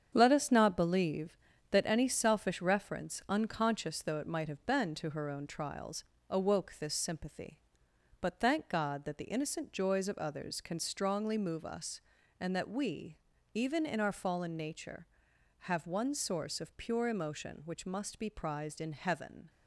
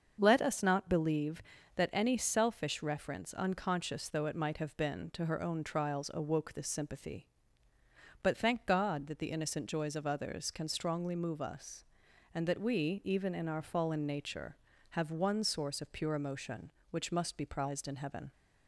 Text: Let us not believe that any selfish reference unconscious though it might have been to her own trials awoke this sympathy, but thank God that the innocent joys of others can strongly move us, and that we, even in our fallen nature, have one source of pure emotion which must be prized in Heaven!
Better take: second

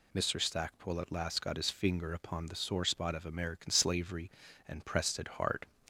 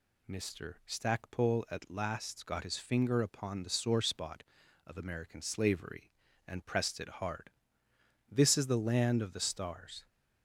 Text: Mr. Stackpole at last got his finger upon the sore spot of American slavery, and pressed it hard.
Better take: first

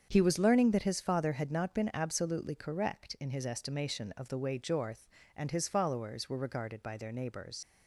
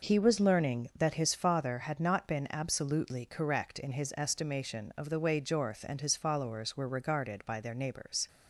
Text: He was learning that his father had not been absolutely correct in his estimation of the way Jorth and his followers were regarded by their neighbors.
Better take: second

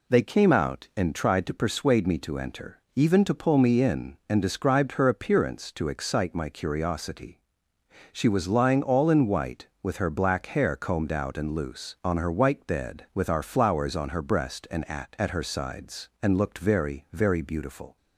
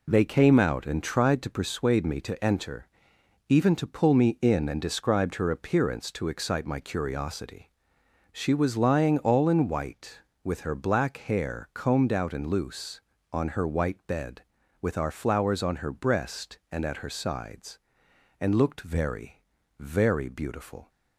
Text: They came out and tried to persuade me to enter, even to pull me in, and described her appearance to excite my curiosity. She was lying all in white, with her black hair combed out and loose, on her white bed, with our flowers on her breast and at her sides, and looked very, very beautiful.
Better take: second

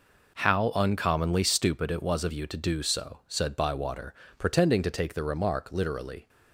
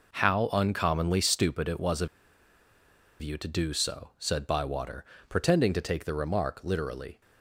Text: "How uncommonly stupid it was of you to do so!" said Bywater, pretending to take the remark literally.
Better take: first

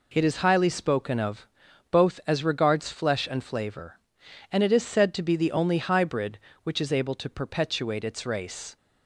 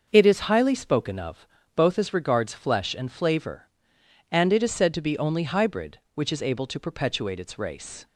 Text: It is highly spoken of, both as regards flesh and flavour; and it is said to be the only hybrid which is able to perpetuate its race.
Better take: first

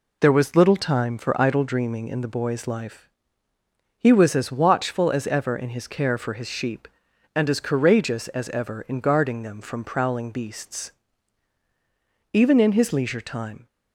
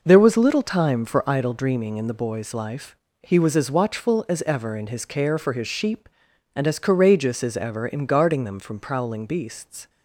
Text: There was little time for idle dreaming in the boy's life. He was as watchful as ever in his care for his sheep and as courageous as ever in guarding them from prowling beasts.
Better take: second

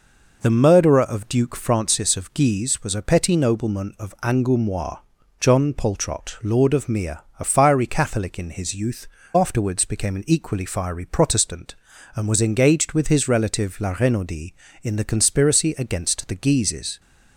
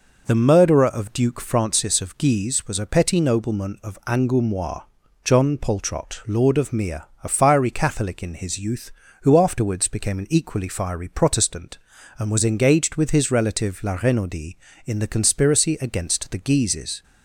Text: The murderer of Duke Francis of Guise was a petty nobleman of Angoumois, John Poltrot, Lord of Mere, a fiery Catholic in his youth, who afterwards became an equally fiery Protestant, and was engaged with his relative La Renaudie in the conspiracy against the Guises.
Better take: second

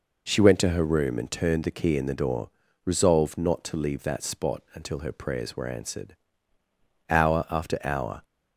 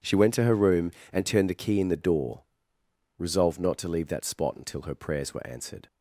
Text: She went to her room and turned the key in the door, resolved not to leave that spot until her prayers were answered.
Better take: second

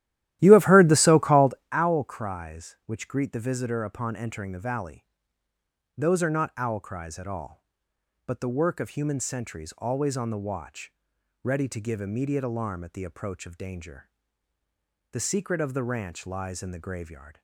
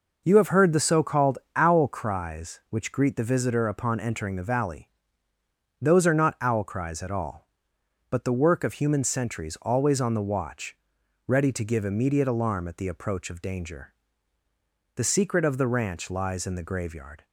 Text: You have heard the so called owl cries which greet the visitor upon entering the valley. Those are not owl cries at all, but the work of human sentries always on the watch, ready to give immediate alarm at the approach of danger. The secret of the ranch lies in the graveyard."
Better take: second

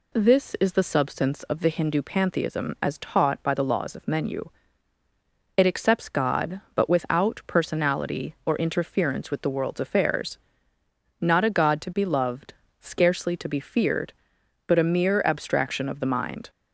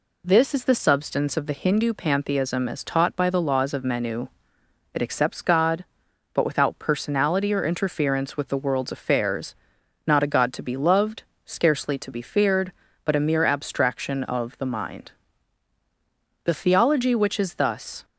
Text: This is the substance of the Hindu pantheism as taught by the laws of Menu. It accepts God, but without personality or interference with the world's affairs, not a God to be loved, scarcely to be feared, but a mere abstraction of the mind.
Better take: first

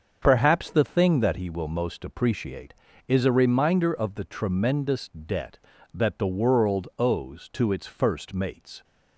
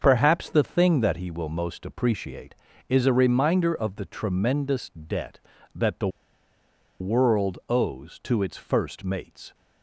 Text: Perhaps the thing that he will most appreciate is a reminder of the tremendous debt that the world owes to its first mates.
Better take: first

